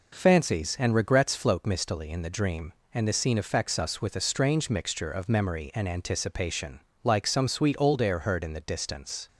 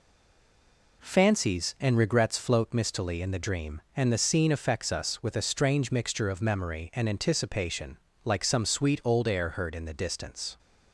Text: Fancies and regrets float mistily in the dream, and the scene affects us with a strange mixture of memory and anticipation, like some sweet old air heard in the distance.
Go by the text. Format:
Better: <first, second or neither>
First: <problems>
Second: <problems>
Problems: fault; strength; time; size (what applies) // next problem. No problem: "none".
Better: first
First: none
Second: stays silent before the first word; until 1.0 s; 1.0 s long